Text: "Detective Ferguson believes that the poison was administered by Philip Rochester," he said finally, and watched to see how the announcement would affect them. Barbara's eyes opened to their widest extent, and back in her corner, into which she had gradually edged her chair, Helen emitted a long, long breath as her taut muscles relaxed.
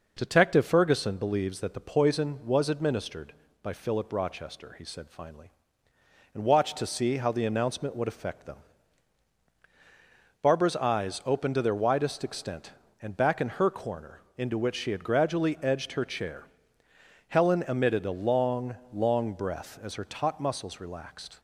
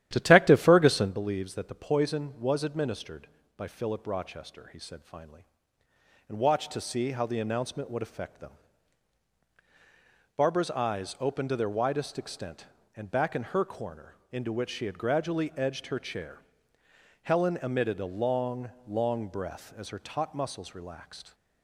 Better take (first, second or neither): first